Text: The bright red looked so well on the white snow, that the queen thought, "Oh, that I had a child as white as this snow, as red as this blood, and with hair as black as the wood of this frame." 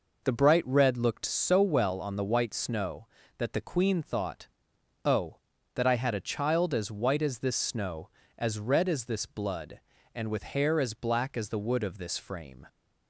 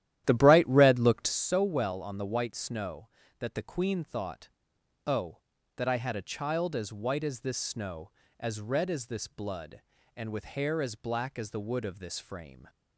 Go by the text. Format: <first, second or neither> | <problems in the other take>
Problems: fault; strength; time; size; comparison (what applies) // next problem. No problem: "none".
first | starts louder than the rest; strong; until 1.4 s; 12.5 dB